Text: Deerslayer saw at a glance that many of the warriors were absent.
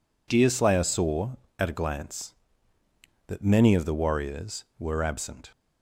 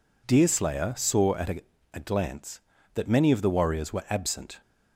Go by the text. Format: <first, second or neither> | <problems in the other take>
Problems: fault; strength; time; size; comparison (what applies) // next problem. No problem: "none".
first | says "a" twice; at 1.9 s